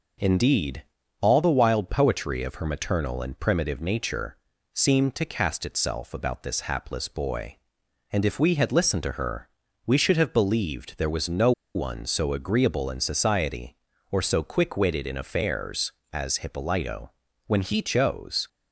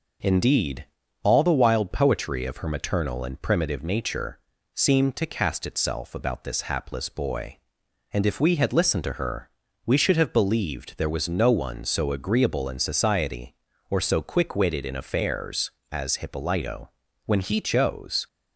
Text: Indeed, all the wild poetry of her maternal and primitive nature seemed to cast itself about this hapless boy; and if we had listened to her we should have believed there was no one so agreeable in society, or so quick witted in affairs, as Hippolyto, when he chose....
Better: second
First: pauses between "nature" and "seemed"; slight; at 4.3 s; 0.36 s long // pauses between "her" and "we"; at 9.4 s; 0.40 s long // pauses between "no" and "one"; slight; at 11.5 s; 0.23 s long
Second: pauses between "nature" and "seemed"; slight; at 4.3 s; 0.34 s long // pauses between "her" and "we"; at 9.4 s; 0.38 s long

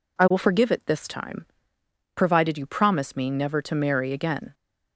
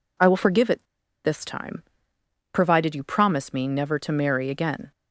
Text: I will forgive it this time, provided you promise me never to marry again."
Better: first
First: none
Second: pauses between "it" and "this"; at 0.8 s; 0.40 s long

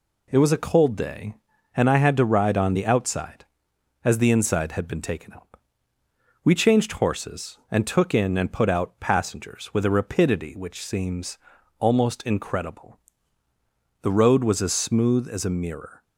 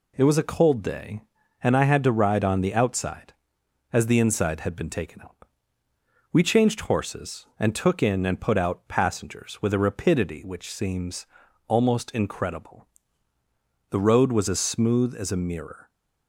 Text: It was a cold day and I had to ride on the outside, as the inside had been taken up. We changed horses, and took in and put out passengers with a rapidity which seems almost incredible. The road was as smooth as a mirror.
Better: neither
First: pauses between "seems" and "almost"; at 11.3 s; 0.42 s long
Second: pauses between "seems" and "almost"; at 11.2 s; 0.42 s long

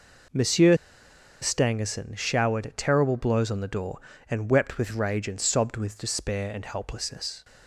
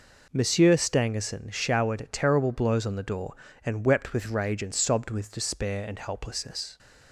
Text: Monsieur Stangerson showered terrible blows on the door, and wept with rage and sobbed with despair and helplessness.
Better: second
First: pauses between "Monsieur" and "Stangerson"; noticeable; at 0.7 s; 0.67 s long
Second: none

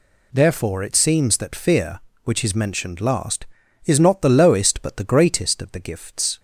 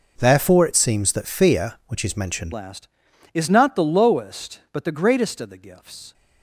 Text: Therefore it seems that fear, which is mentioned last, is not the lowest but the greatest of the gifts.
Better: first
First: none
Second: changes voice at "last"; from 2.5 s on; 3.6 s long

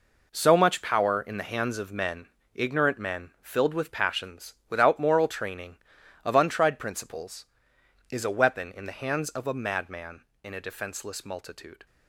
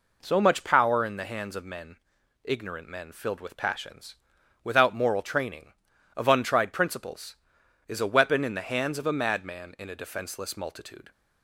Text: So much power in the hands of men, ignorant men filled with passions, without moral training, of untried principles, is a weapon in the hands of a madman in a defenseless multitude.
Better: second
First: gets quieter; strong; throughout; 10 dB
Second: none

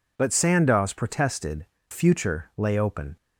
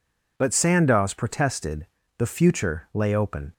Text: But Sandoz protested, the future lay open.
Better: second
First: skips "the"; at 1.7 s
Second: none

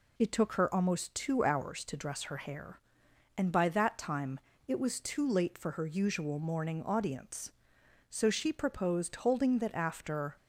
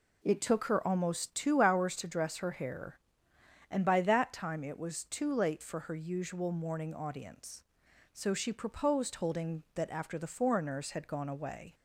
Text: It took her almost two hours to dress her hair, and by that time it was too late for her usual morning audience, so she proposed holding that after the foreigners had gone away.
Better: second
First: pauses between "time" and "it"; slight; at 4.3 s; 0.26 s long // stops before "the foreigners had gone away"; at 10.3 s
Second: none

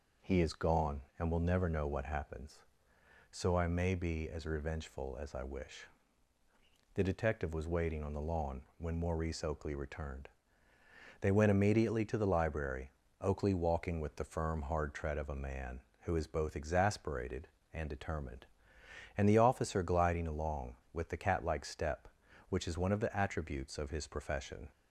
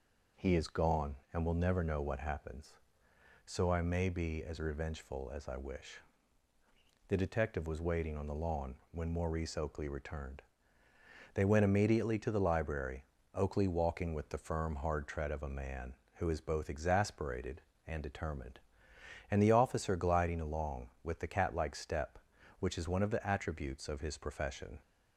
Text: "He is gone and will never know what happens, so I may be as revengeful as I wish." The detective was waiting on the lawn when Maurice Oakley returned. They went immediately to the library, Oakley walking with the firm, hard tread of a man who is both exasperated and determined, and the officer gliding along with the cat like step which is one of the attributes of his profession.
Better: neither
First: pauses between "lawn" and "when"; slight; at 8.6 s; 0.16 s long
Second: pauses between "lawn" and "when"; slight; at 8.7 s; 0.16 s long

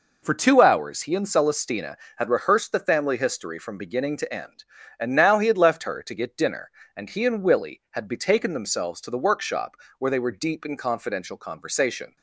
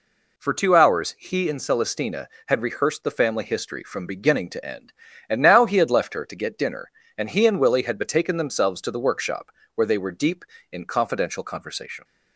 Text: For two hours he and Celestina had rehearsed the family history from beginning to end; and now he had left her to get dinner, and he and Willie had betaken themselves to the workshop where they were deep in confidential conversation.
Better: neither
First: pauses between "workshop" and "where"; slight; at 9.7 s; 0.22 s long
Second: pauses between "workshop" and "where"; slight; at 9.4 s; 0.26 s long

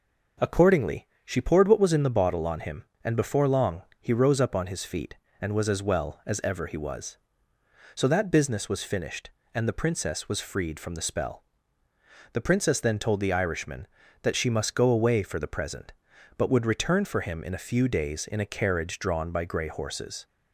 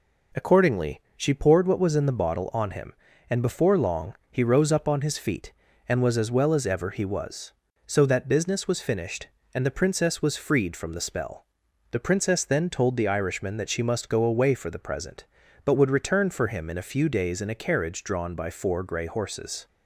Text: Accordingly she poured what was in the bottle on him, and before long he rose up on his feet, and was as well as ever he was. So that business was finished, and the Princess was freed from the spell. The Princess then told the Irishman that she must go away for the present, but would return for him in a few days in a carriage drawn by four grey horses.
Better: second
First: pauses between "Accordingly" and "she"; slight; at 1.0 s; 0.18 s long // pauses between "long" and "he"; slight; at 3.8 s; 0.18 s long // skips "four"; at 19.4 s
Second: pauses between "long" and "he"; slight; at 4.1 s; 0.16 s long

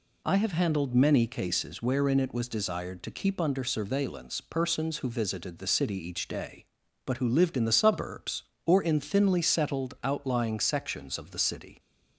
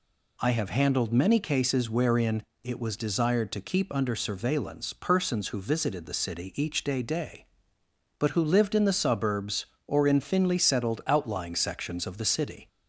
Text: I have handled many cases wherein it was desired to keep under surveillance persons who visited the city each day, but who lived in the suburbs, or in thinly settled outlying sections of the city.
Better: first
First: none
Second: pauses between "wherein" and "it"; slight; at 2.4 s; 0.18 s long // says "day" twice; at 7.0 s

